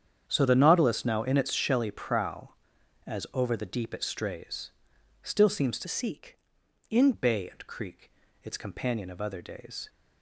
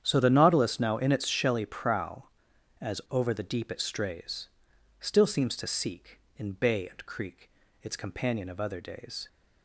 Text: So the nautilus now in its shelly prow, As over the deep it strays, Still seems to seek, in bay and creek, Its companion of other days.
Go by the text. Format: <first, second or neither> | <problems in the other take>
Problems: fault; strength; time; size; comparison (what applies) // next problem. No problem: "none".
second | starts louder than the rest; strong; until 1.2 s; 8 dB; strong in the second // changes voice from "seek" to "in"; from 5.8 to 7.1 s; 1.3 s long